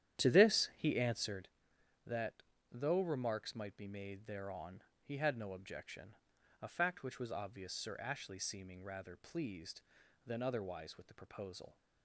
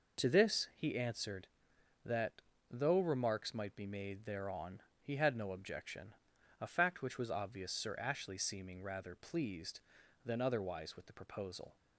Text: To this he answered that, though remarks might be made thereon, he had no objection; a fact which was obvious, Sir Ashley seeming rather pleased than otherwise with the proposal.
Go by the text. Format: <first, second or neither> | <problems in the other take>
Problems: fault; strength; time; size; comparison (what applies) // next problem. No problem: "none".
second | starts louder than the rest; strong; until 1.6 s; 11 dB